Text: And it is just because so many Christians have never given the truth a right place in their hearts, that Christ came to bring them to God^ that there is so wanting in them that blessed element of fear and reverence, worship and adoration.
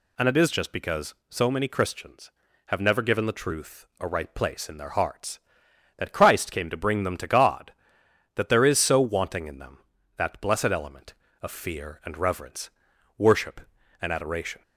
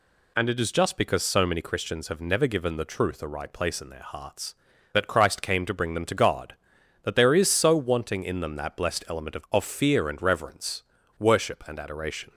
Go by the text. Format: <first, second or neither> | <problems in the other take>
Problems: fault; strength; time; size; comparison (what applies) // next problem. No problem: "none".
first | says "of" twice; at 9.4 s